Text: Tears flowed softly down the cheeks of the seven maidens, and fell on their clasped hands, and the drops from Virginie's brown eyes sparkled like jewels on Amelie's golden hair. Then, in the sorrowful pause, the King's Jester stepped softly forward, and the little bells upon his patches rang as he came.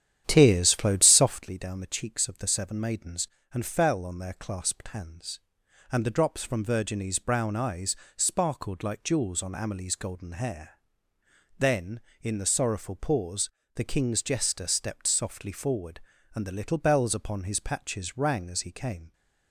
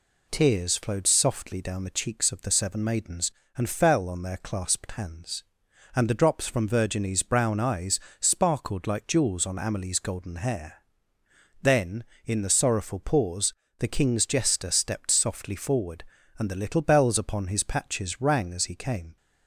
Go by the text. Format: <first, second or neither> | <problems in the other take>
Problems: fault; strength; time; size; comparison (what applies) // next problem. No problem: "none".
second | starts louder than the rest; strong; until 1.5 s; 10 dB // pauses between "eyes" and "sparkled"; slight; at 7.9 s; 0.22 s long; slight in the second